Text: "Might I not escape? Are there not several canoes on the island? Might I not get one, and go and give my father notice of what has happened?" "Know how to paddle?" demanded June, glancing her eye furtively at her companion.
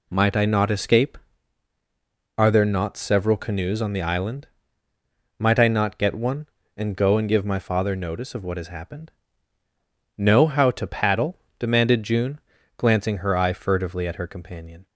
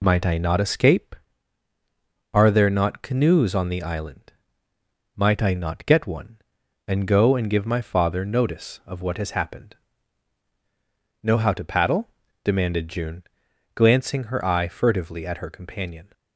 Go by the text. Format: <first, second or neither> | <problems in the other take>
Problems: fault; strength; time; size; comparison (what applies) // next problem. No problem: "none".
first | skips "several"; at 3.0 s